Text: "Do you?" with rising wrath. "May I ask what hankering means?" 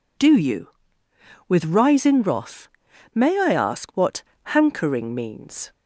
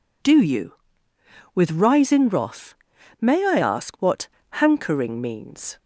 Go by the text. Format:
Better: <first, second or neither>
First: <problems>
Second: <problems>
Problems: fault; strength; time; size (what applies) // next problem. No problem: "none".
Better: neither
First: pauses between "what" and "hankering"; slight; at 4.2 s; 0.20 s long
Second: pauses between "what" and "hankering"; slight; at 4.2 s; 0.22 s long